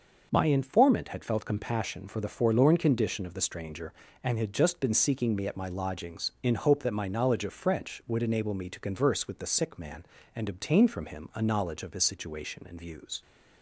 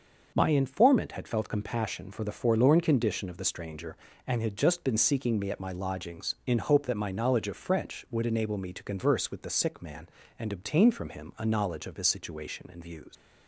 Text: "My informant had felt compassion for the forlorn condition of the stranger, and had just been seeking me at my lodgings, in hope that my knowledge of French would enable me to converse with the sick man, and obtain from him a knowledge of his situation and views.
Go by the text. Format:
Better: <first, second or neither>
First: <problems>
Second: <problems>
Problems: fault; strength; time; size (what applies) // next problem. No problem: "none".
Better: first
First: none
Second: leaves "views" unfinished; at 13.1 s; 95 ms